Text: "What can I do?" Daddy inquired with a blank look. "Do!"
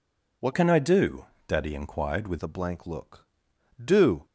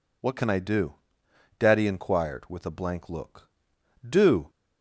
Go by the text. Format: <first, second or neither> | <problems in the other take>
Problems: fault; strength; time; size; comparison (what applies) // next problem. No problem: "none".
second | changes voice from "can" to "with"; from 0.5 to 2.3 s; 1.8 s long